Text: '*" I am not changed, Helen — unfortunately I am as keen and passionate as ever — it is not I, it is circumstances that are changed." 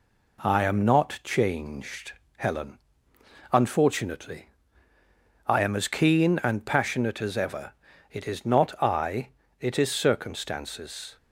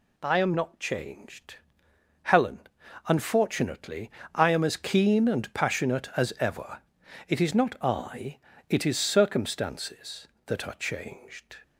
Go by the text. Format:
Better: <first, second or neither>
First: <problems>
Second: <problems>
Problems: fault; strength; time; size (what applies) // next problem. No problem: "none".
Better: second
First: pauses between "unfortunately" and "I"; noticeable; at 4.4 s; 0.98 s long // stops before "that are changed"; at 11.1 s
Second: pauses between "unfortunately" and "I"; slight; at 4.1 s; 0.20 s long